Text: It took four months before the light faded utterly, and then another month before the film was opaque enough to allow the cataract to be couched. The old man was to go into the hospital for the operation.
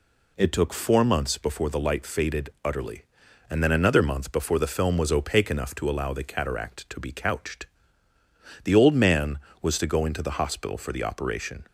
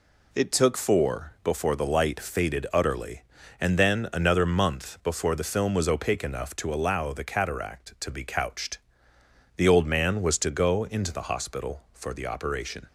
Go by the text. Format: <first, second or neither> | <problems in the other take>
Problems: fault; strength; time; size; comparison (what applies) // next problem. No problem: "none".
first | skips "months"; at 1.3 s